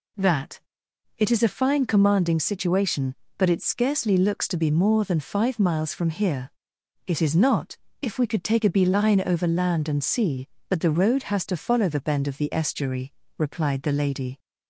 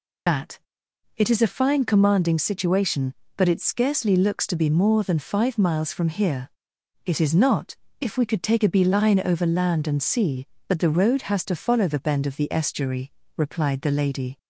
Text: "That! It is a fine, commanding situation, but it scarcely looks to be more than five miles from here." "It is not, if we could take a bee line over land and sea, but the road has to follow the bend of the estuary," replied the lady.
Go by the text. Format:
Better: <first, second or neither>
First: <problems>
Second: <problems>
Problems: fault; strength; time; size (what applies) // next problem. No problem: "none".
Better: first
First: none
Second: loses the start of "That"; at 0.2 s; 110 ms